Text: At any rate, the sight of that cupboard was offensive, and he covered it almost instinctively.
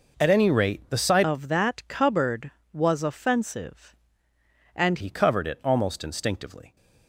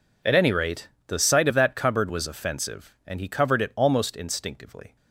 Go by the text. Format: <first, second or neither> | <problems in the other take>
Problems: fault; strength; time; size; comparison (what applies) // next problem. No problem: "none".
second | changes voice from "of" to "and"; from 1.2 to 4.9 s; 3.7 s long